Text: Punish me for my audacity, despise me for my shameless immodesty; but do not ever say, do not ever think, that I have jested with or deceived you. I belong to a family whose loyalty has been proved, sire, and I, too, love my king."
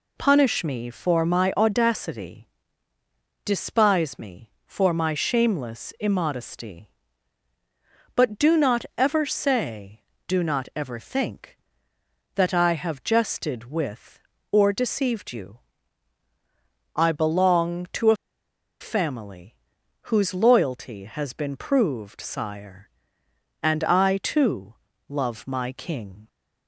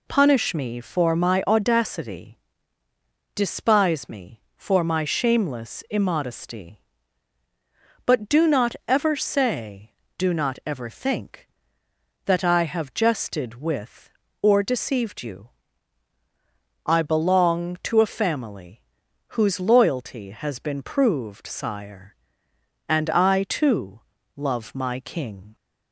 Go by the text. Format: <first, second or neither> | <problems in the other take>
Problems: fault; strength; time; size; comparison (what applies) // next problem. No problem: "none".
second | pauses between "a" and "family"; noticeable; at 18.1 s; 0.65 s long // pauses between "family" and "whose"; noticeable; at 19.5 s; 0.52 s long; noticeable in the second